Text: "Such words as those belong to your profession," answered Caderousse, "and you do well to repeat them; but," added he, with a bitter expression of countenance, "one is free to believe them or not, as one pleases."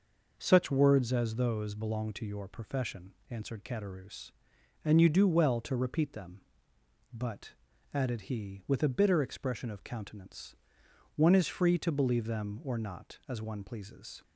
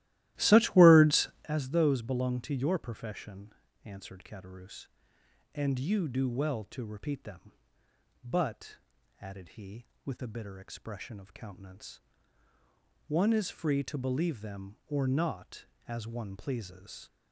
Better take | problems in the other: first | starts louder than the rest; strong; until 1.5 s; 15.5 dB

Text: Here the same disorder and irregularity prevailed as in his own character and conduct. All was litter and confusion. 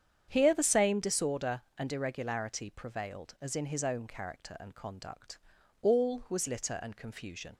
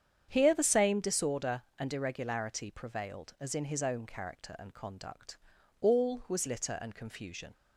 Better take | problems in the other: neither | starts louder than the rest; strong; the same in both

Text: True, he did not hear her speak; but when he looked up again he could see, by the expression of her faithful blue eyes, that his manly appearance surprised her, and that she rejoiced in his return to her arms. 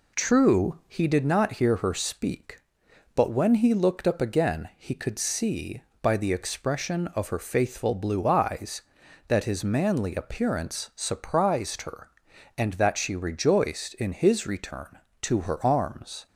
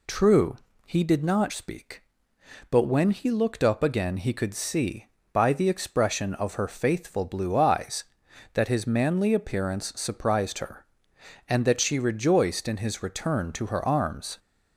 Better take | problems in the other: first | skips "hear her"; at 1.5 s

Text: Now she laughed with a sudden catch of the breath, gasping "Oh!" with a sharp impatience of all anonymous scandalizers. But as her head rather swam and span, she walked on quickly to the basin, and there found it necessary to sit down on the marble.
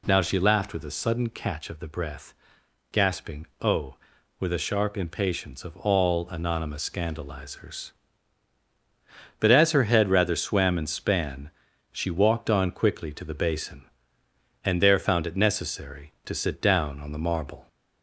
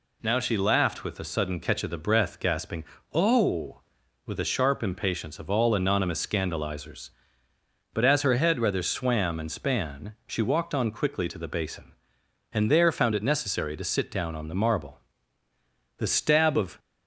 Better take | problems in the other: first | pauses between "gasping" and "Oh"; slight; at 2.8 s; 0.26 s long; slight in the first // goes on to say "The stab of"; noticeable; from 15.9 s on; 0.80 s long

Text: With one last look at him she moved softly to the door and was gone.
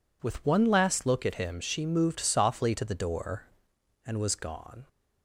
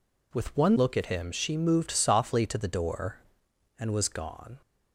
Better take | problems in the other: first | skips "last"; at 0.7 s

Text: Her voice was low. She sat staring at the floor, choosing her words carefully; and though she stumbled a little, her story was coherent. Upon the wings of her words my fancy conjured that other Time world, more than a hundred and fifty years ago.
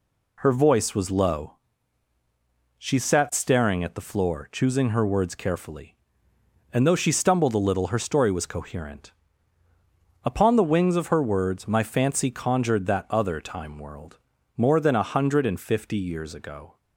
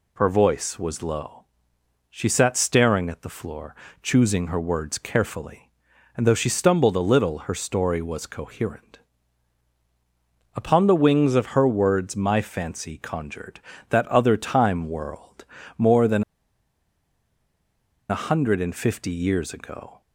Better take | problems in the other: first | pauses between "than" and "a"; strong; at 16.2 s; 1.8 s long

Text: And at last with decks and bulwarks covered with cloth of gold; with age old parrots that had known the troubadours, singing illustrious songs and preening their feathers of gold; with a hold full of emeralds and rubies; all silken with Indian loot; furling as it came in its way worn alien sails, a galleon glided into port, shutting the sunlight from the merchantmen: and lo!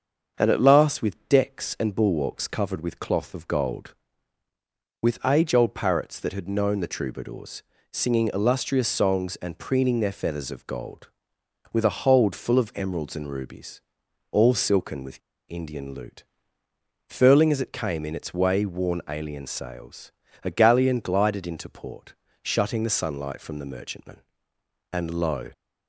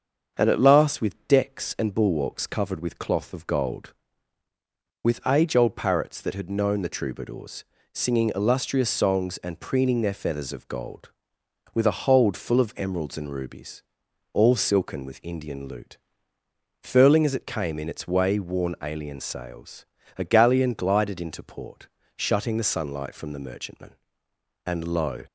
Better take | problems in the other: second | starts louder than the rest; until 1.3 s; 6.5 dB; also in the second // pauses between "with" and "Indian"; slight; at 15.2 s; 0.30 s long

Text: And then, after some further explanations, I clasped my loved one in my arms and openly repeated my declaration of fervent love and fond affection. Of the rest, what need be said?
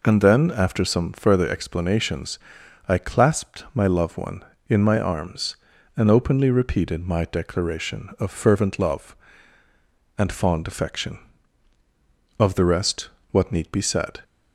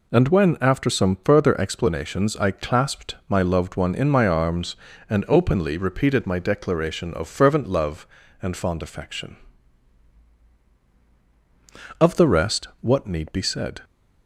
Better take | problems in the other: first | says "when" for "then"; at 0.2 s

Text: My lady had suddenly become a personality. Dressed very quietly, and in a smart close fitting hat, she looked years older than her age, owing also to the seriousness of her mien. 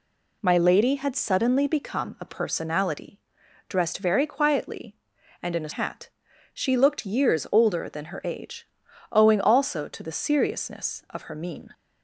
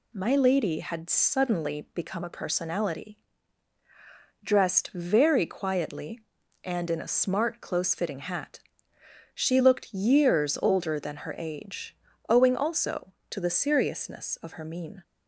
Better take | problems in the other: second | skips "smart close fitting"; at 5.7 s

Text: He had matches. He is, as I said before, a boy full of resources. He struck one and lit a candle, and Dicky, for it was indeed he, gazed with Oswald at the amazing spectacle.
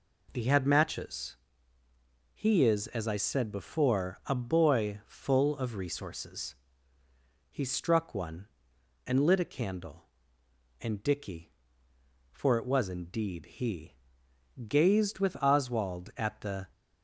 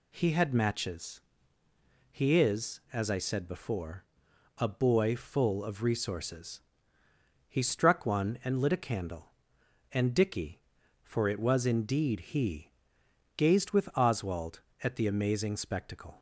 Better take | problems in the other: second | stops before "amazing spectacle"; at 16.7 s

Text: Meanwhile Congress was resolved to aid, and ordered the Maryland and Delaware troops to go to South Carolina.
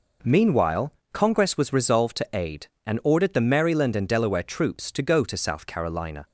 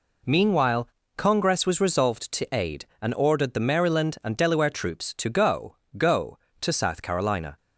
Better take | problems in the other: first | pauses between "Meanwhile" and "Congress"; slight; at 0.8 s; 0.28 s long; slight in the first // says "go" twice; at 5.9 s

